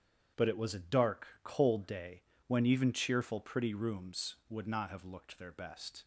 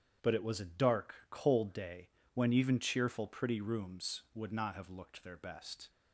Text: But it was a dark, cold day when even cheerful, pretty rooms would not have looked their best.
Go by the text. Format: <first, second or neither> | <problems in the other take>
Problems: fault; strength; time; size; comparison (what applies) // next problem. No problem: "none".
neither | starts louder than the rest; strong; the same in both // pauses between "day" and "when"; slight; the same in both